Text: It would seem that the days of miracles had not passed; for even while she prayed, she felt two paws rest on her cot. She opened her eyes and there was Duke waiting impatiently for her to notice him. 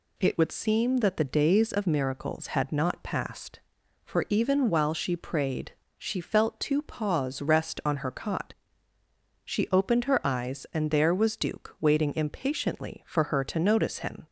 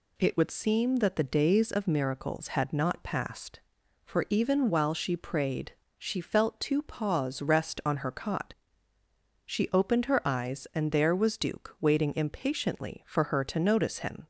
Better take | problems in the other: neither | none

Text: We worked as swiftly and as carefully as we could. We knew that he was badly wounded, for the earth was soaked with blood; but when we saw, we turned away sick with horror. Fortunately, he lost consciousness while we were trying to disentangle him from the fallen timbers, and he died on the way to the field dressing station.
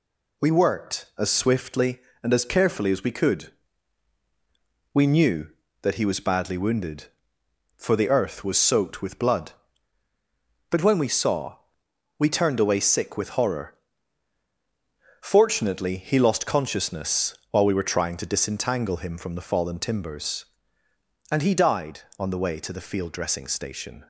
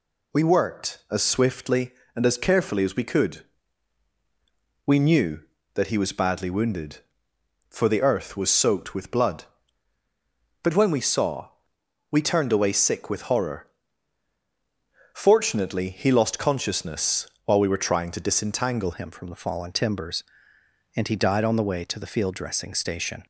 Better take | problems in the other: first | changes voice at "him"; from 18.9 s on; 4.3 s long

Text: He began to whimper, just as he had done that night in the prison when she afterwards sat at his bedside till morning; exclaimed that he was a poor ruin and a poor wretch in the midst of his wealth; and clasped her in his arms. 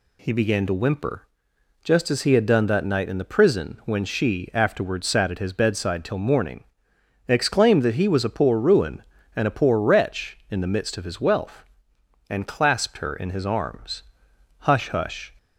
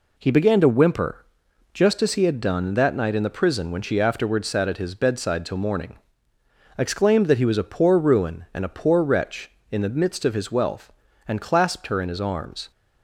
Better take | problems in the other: second | goes on to say "Hush hush"; noticeable; from 14.6 s on; 0.68 s long

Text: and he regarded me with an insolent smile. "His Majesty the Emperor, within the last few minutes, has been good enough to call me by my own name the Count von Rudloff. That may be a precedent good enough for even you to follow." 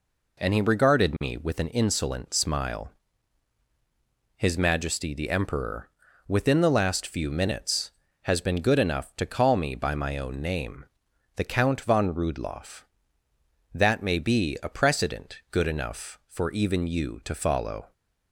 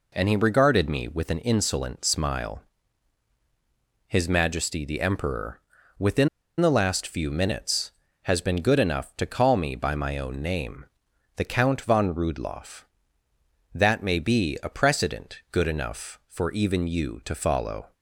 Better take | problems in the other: first | pauses between "within" and "the"; slight; at 6.2 s; 0.32 s long // pauses between "name" and "the"; noticeable; at 10.8 s; 0.52 s long; noticeable in the first

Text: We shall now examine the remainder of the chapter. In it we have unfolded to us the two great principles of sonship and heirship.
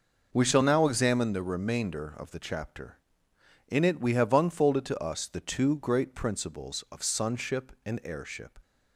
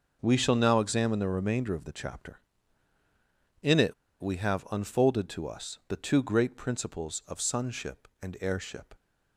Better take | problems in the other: first | starts louder than the rest; noticeable; until 1.2 s; 6 dB // pauses between "it" and "we"; slight; at 3.9 s; 0.27 s long

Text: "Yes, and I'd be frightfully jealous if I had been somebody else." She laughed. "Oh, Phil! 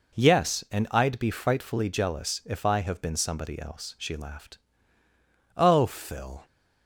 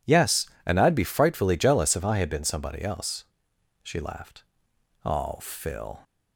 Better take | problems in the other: second | says "have" for "had"; at 2.8 s

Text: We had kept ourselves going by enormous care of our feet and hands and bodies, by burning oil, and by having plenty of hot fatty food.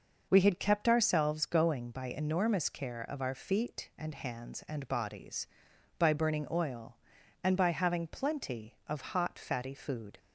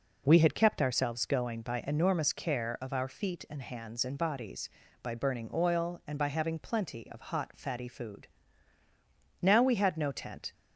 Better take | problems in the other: first | goes on to say "Now we had no tent"; noticeable; from 9.4 s on; 1.1 s long

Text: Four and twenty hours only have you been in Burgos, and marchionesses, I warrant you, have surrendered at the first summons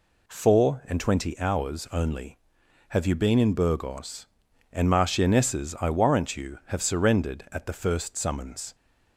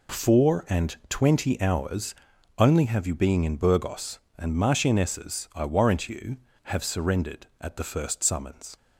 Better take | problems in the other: first | pauses between "hours" and "only"; at 2.1 s; 0.42 s long // says "being" for "been"; at 3.1 s

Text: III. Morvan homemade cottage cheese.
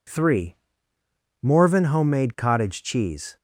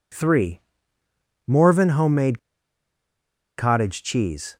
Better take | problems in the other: first | pauses between "homemade" and "cottage"; at 2.3 s; 1.1 s long

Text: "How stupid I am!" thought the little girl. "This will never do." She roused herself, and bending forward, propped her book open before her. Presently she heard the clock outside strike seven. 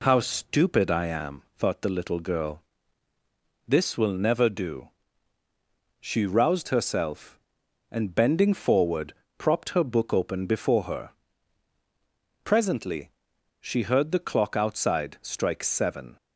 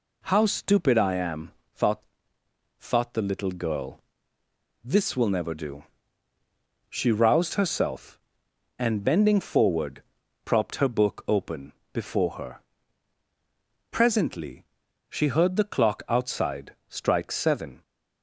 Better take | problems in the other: first | says "thought" twice; at 2.7 s // pauses between "open" and "before"; slight; at 11.7 s; 0.20 s long // pauses between "Presently" and "she"; noticeable; at 14.6 s; 0.46 s long; noticeable in the first

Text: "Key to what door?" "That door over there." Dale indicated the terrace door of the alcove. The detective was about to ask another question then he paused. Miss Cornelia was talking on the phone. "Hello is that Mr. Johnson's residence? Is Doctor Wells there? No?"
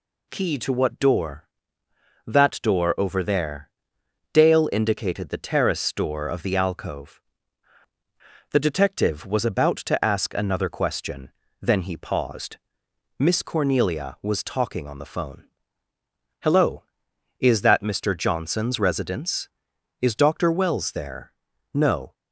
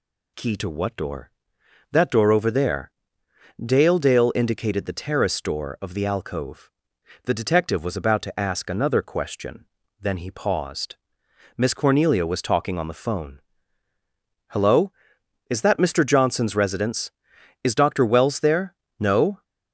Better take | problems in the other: first | says "Dale" twice; at 3.9 s // pauses between "question" and "then"; slight; at 9.6 s; 0.36 s long; slight in the first

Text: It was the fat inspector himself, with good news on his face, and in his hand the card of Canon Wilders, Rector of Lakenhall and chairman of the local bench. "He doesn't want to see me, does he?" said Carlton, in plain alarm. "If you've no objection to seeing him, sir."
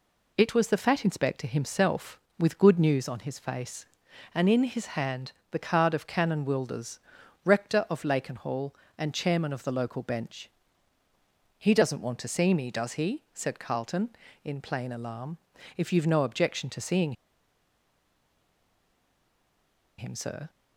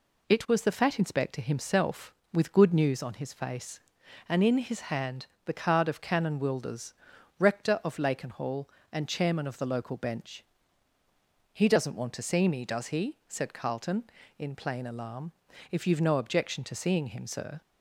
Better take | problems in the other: second | pauses between "hand" and "the"; slight; at 5.3 s; 0.20 s long; slight in the second // pauses between "seeing" and "him"; strong; at 17.1 s; 2.8 s long

